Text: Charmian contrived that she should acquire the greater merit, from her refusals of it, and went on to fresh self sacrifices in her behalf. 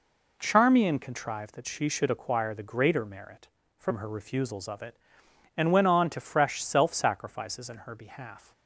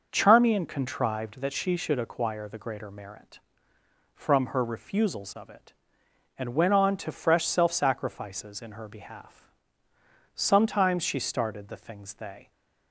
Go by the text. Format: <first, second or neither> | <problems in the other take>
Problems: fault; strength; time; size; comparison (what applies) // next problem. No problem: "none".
first | starts louder than the rest; noticeable; until 1.1 s; 6 dB // goes on to say "Sometimes she started the things they"; strong; from 10.3 s on; 2.1 s long